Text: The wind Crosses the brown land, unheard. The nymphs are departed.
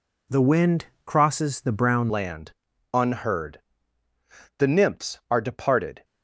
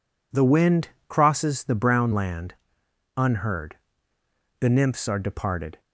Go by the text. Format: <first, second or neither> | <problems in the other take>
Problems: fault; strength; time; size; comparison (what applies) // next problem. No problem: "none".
second | pauses between "wind" and "Crosses"; slight; at 0.8 s; 0.20 s long; slight in the second // changes voice at "land"; from 2.0 s on; 4.0 s long